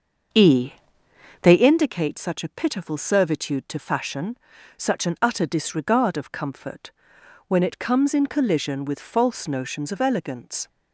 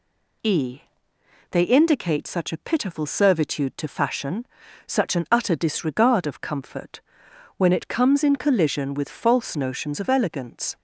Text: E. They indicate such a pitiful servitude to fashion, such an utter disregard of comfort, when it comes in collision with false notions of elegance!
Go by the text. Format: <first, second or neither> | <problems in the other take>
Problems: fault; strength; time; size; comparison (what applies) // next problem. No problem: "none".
second | starts louder than the rest; until 1.7 s; 6.5 dB